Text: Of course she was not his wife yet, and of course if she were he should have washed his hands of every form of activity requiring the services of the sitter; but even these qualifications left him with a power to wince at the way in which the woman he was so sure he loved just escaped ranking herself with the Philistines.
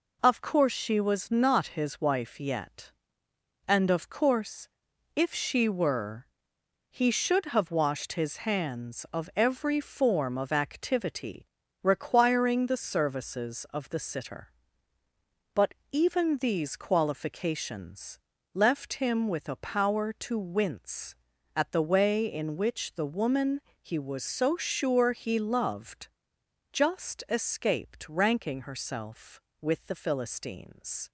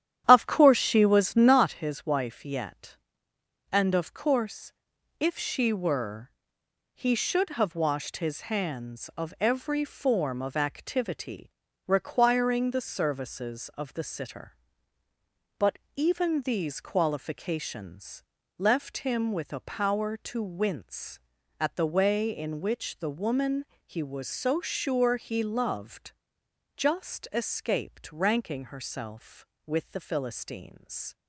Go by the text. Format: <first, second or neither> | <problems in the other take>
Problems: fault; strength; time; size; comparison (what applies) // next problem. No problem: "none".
first | starts louder than the rest; strong; until 1.7 s; 10.5 dB // pauses between "course" and "if"; noticeable; at 4.7 s; 0.48 s long; noticeable in the first // pauses between "were" and "he"; noticeable; at 6.2 s; 0.66 s long; noticeable in the first // pauses between "activity" and "requiring"; at 11.4 s; 0.38 s long; also in the first // pauses between "but" and "even"; slight; at 15.7 s; 0.16 s long; slight in the first // pauses between "qualifications" and "left"; slight; at 18.2 s; 0.34 s long; slight in the first // pauses between "woman" and "he"; slight; at 23.6 s; 0.20 s long; slight in the first // pauses between "loved" and "just"; noticeable; at 26.1 s; 0.64 s long; noticeable in the first